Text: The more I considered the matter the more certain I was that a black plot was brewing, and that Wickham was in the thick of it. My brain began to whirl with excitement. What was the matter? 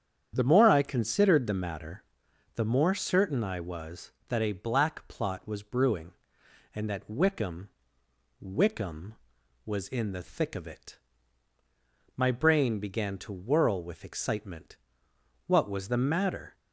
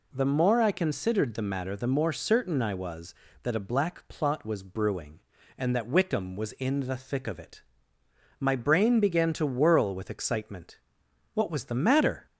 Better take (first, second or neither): second